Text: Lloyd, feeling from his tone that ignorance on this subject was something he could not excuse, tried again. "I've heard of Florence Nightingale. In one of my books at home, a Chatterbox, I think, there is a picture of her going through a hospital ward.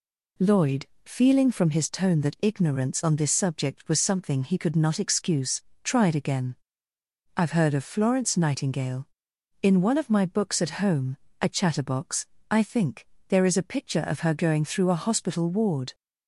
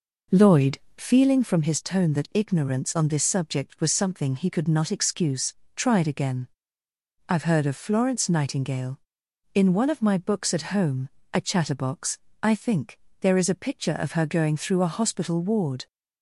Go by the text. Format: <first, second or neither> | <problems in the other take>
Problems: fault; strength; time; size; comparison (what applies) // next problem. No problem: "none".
first | starts louder than the rest; noticeable; until 1.2 s; 5 dB